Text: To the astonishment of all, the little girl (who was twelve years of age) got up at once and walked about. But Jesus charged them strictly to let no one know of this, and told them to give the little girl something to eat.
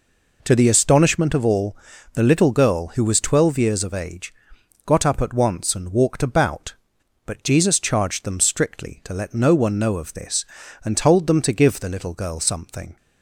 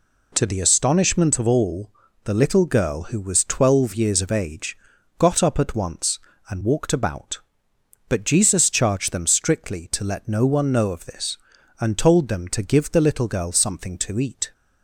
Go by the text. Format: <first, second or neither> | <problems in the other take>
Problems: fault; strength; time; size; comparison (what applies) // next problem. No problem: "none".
second | stops before "to eat"; at 12.9 s